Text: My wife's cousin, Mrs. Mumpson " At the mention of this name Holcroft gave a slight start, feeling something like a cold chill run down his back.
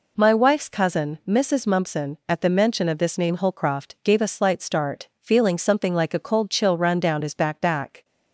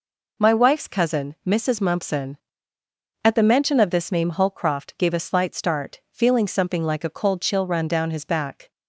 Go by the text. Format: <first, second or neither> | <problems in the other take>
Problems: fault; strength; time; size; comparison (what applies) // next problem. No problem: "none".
second | says "back" twice; at 7.5 s